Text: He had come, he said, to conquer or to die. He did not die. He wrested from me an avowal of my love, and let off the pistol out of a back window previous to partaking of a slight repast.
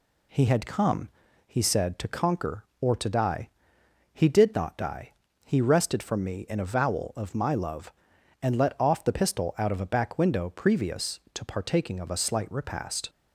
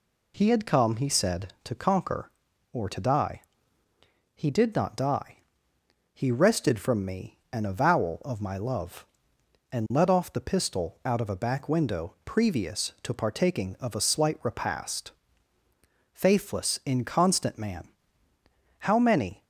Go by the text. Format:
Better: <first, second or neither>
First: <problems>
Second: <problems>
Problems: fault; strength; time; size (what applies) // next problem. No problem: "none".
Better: first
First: none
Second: pauses between "me" and "an"; slight; at 7.3 s; 0.16 s long // goes on to say "Faithless inconstant man How many"; strong; from 16.1 s on; 3.3 s long